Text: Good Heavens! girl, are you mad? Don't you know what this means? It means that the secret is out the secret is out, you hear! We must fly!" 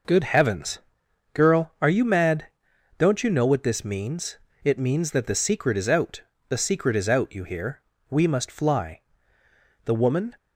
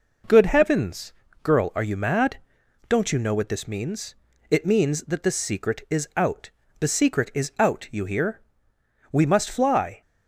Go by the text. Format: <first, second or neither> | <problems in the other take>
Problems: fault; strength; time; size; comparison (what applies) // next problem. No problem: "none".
second | pauses between "out" and "the"; slight; at 6.2 s; 0.26 s long; slight in the second // goes on to say "The woman"; from 9.8 s on; 0.50 s long